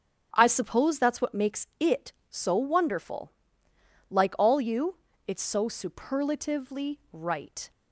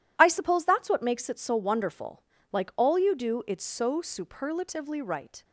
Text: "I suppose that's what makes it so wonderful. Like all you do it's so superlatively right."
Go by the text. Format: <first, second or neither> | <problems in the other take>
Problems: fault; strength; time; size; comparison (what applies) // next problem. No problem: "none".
second | starts louder than the rest; strong; until 1.3 s; 7.5 dB // skips "do"; at 5.1 s